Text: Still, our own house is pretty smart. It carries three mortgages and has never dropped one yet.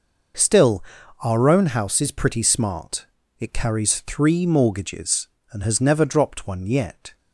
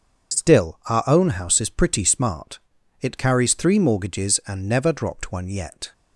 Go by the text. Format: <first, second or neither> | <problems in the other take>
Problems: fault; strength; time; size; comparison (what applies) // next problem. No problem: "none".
first | starts louder than the rest; until 1.4 s; 7 dB // skips "has"; at 4.6 s